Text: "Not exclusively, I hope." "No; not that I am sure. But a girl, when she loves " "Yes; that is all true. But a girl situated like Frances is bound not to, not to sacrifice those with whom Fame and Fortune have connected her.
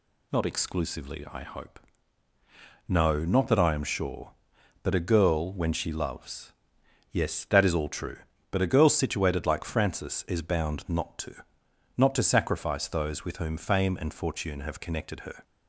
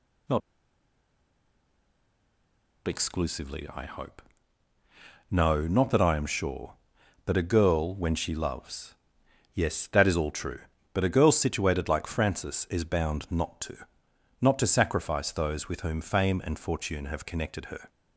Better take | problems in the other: first | pauses between "Not" and "exclusively"; strong; at 0.4 s; 2.4 s long

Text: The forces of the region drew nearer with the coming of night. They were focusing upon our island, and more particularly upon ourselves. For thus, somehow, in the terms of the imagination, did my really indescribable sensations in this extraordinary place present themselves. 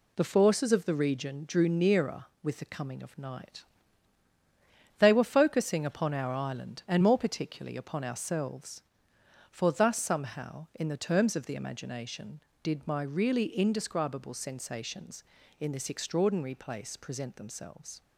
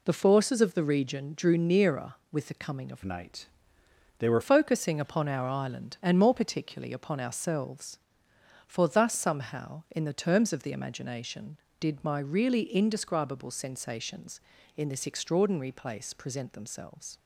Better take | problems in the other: first | changes voice from "night" to "were"; from 3.0 to 4.4 s; 1.4 s long

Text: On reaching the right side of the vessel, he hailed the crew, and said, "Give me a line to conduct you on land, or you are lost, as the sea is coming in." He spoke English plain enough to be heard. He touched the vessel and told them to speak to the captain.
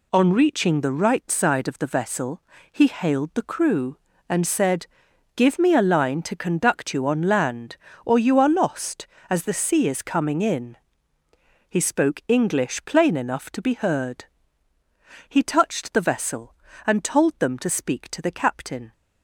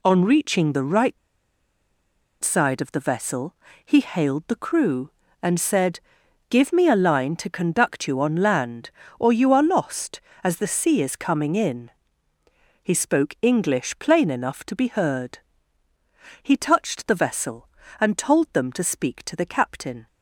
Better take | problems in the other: first | pauses between "right" and "side"; at 1.1 s; 1.2 s long

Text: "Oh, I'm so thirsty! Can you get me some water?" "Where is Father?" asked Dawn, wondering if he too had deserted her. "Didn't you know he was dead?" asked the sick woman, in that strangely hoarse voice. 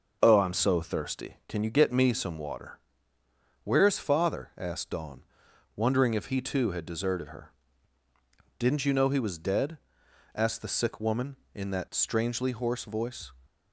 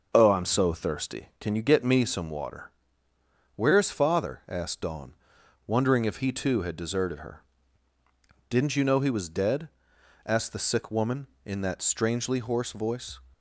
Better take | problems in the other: neither | none

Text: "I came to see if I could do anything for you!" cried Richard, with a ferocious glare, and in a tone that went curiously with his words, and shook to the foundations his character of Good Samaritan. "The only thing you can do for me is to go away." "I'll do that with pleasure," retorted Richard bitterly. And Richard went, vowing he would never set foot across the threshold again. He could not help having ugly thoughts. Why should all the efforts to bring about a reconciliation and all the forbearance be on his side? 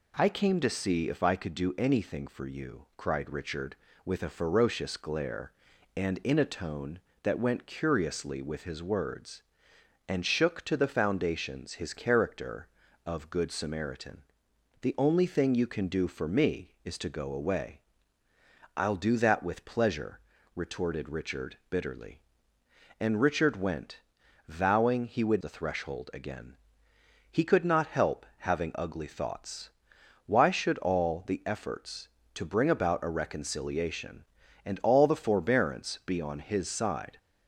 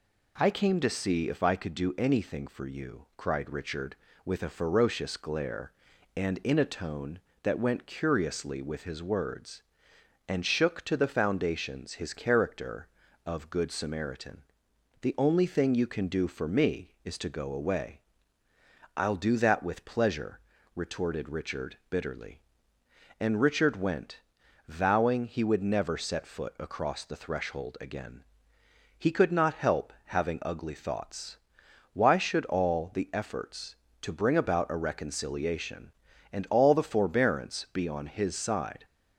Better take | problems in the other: second | skips "never set foot across"; at 25.4 s

